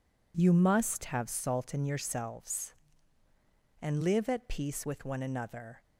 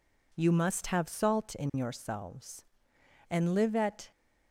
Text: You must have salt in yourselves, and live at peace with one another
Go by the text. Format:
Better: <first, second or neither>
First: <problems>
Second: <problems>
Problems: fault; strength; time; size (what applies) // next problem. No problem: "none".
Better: first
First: none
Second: stops before "peace with one another"; at 4.1 s